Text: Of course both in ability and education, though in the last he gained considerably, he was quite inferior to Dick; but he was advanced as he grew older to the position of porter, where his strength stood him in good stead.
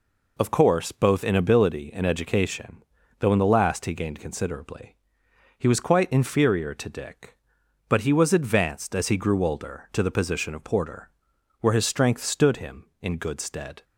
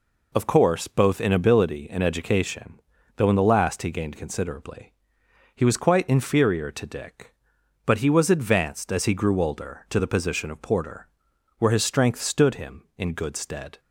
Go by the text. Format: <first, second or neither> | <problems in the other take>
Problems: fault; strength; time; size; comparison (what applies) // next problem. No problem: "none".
neither | none